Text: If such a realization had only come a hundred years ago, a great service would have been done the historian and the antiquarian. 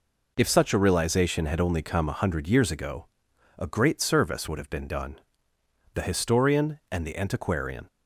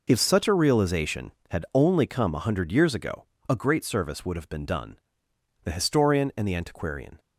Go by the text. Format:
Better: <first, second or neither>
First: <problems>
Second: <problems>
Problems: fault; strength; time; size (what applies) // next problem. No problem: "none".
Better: neither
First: pauses between "done" and "the"; noticeable; at 5.1 s; 0.74 s long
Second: pauses between "done" and "the"; noticeable; at 4.9 s; 0.68 s long